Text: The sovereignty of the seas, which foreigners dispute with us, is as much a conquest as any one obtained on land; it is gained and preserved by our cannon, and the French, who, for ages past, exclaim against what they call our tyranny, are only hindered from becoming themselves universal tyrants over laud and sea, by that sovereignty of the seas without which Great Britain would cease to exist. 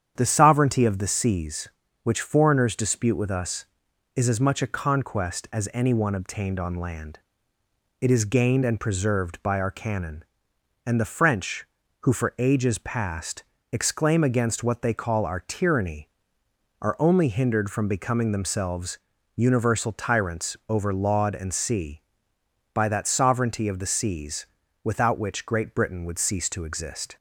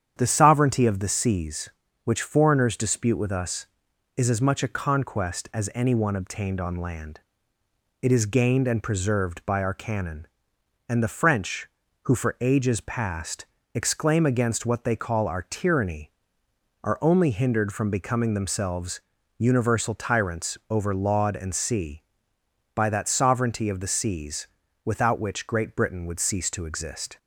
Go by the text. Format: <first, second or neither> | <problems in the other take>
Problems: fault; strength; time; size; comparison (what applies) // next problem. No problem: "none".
neither | starts louder than the rest; strong; the same in both // pauses between "themselves" and "universal"; slight; the same in both // pauses between "seas" and "without"; the same in both